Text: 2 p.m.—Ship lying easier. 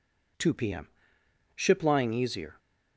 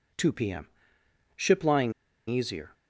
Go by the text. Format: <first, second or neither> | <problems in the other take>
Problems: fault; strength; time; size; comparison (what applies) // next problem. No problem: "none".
first | pauses between "lying" and "easier"; at 1.9 s; 0.37 s long